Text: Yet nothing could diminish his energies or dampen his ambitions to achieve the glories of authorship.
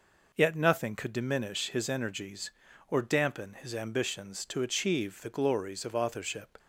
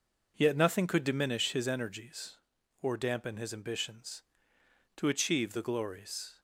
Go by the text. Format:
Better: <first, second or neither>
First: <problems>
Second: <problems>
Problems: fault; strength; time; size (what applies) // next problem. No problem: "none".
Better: first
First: none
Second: stops before "of authorship"; at 6.3 s